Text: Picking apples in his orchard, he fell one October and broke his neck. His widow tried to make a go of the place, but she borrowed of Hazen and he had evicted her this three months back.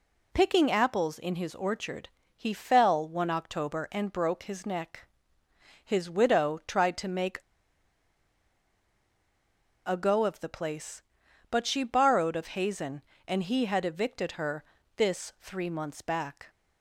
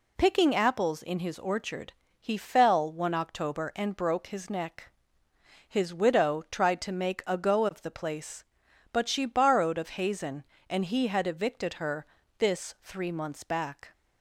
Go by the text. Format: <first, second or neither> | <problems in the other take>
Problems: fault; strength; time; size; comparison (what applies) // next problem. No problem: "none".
second | pauses between "make" and "a"; strong; at 7.3 s; 2.4 s long // pauses between "her" and "this"; slight; at 14.6 s; 0.34 s long; slight in the second